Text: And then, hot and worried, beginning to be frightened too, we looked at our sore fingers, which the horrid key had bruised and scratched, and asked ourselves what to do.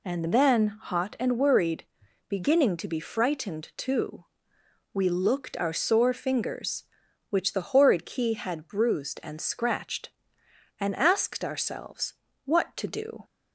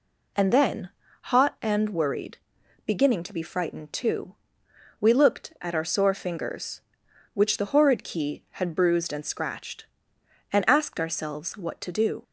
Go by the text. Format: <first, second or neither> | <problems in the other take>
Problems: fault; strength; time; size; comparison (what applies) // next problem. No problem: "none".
second | skips "at"; at 5.5 s // pauses between "ourselves" and "what"; slight; at 12.1 s; 0.30 s long